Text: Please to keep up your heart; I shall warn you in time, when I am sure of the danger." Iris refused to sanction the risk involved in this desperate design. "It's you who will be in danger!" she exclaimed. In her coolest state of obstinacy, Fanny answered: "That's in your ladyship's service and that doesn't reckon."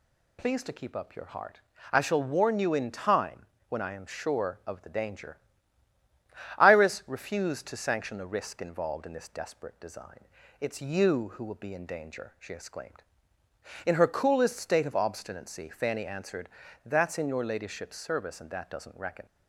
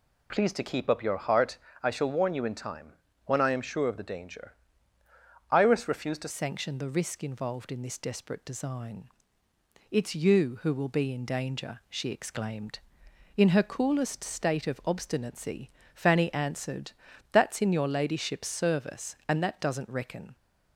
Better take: first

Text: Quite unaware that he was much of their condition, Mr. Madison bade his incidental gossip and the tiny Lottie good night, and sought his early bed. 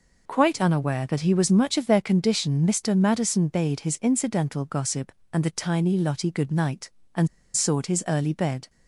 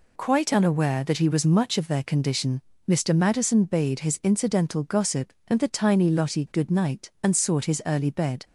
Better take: second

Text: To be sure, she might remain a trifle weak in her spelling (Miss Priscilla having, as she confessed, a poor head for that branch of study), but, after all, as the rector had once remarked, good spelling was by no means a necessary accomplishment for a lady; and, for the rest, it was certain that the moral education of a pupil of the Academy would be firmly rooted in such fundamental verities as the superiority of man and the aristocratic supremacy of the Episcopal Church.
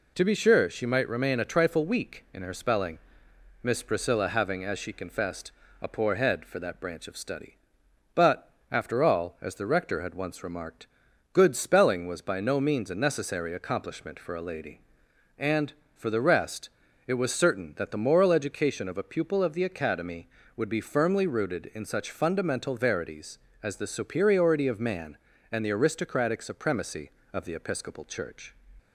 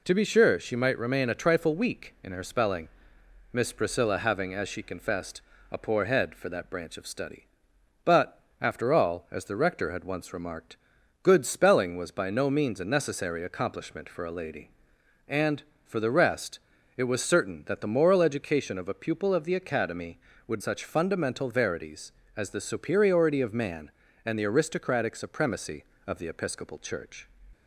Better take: first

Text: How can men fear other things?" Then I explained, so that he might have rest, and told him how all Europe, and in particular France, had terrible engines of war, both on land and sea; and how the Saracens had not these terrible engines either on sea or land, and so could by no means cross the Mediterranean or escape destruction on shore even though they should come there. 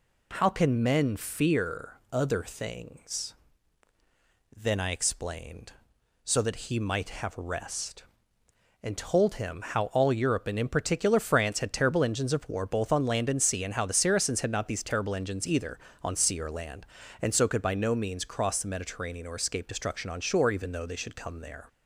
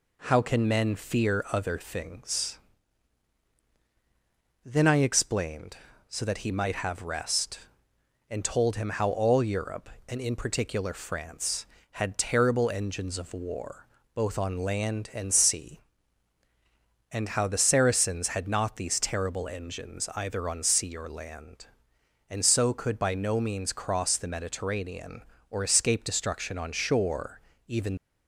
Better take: first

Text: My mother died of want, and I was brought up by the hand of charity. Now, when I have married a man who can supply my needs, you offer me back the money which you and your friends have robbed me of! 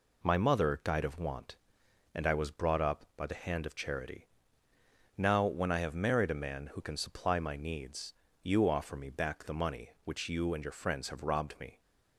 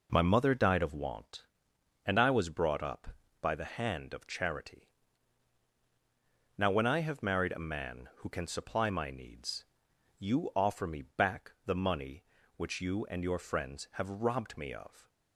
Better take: second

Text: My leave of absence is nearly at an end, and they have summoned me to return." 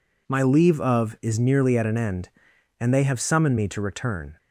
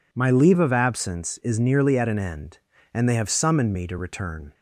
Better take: second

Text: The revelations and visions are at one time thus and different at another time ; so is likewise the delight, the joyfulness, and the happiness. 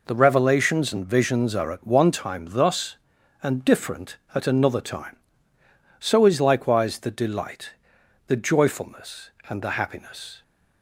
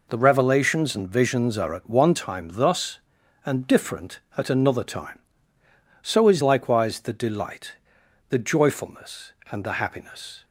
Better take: neither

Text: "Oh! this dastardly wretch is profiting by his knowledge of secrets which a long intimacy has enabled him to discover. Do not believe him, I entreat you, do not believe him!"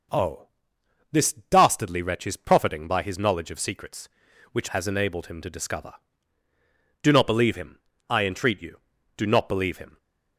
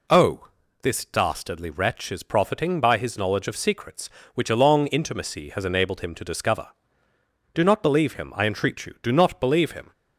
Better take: second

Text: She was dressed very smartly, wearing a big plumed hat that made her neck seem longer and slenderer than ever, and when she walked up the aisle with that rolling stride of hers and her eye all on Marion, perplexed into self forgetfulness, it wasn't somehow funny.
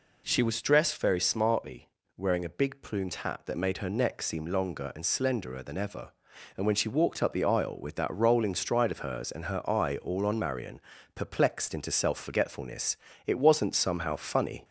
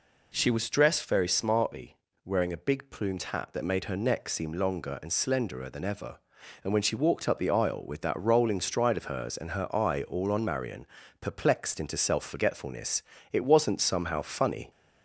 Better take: neither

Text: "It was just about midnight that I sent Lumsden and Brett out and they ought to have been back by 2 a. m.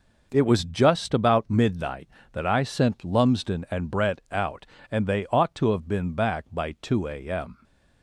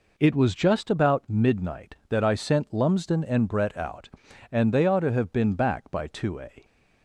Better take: first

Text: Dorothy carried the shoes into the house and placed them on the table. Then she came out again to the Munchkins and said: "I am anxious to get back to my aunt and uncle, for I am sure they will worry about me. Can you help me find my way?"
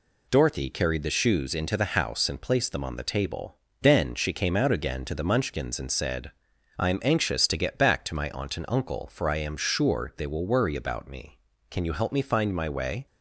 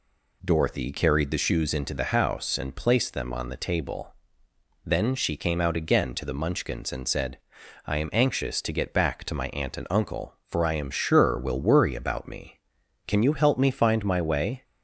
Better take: first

